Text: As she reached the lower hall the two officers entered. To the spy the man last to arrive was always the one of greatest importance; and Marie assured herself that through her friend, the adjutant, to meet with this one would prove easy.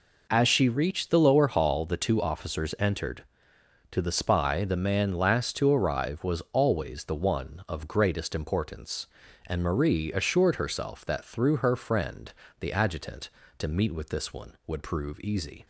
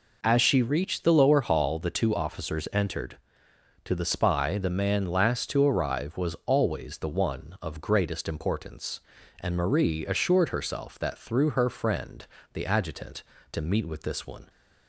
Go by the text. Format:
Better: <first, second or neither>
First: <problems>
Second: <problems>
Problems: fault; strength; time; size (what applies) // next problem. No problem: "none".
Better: first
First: none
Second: stops before "would prove easy"; at 14.4 s